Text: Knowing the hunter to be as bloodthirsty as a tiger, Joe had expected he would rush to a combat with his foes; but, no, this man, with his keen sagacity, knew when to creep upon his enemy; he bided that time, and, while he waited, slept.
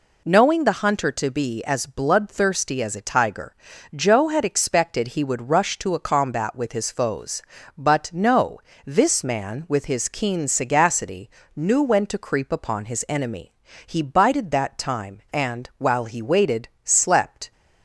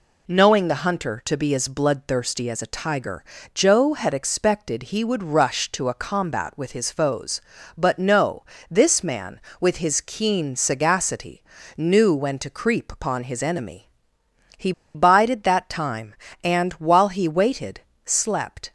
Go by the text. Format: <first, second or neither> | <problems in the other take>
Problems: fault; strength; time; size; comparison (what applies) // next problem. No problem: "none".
first | pauses between "he" and "bided"; slight; at 14.7 s; 0.23 s long